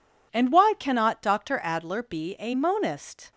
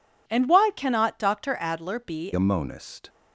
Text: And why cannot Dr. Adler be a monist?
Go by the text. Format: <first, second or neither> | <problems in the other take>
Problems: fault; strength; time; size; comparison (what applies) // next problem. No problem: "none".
first | changes voice at "a"; from 2.3 s on; 0.7 s long